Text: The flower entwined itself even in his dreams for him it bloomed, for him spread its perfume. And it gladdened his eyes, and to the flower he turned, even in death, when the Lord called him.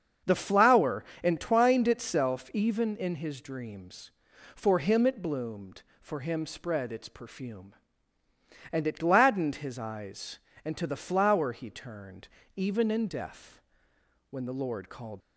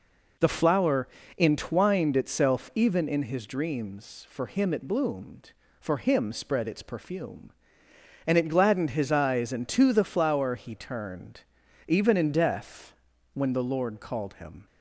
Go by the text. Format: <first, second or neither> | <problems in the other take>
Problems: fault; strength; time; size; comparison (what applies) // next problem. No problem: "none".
second | starts louder than the rest; until 1.4 s; 6.5 dB // pauses between "flower" and "entwined"; slight; at 1.0 s; 0.20 s long; slight in the second // stops before "him"; at 15.2 s